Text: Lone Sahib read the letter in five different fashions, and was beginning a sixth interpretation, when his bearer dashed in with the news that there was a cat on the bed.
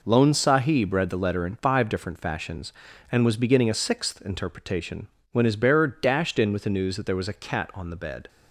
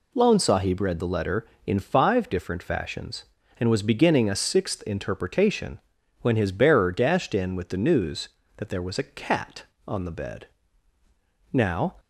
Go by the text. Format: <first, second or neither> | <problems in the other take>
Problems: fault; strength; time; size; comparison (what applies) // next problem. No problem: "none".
first | goes on to say "Now"; slight; from 11.5 s on; 0.46 s long